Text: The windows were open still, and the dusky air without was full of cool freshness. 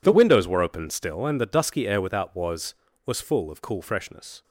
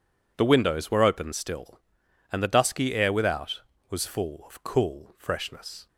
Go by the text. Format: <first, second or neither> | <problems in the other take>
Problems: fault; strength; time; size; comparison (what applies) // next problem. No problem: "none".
second | says "was" twice; at 3.0 s